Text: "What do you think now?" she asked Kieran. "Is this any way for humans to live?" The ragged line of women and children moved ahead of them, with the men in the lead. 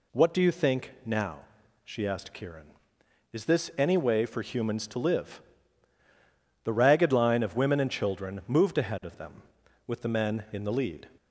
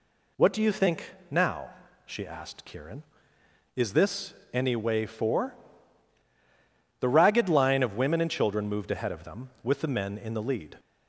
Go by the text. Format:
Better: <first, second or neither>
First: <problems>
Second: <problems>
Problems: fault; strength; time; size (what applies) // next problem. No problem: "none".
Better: first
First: none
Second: pauses between "think" and "now"; slight; at 1.1 s; 0.18 s long // pauses between "this" and "any"; slight; at 4.3 s; 0.18 s long // skips "humans to live"; at 6.2 s